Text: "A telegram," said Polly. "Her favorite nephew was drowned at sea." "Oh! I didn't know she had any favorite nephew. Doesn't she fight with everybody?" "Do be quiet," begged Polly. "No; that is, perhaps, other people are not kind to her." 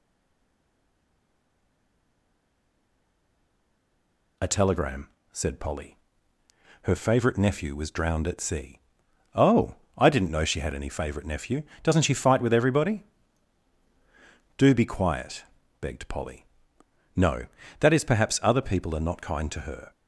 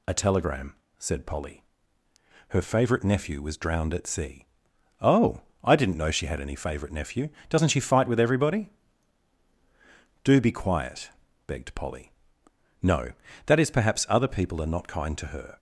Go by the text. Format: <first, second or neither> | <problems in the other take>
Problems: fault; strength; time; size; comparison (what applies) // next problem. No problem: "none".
second | stays silent before the first word; strong; until 4.3 s; 4.3 s long